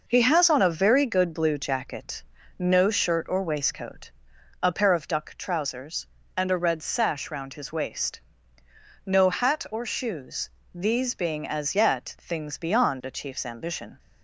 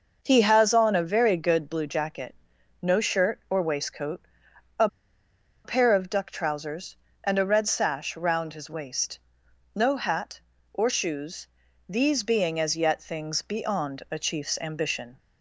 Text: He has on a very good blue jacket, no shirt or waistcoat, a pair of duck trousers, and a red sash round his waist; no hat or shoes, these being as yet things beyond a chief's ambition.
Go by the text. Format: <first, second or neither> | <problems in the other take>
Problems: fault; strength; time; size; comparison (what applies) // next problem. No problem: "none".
first | pauses between "a" and "pair"; noticeable; at 4.8 s; 0.77 s long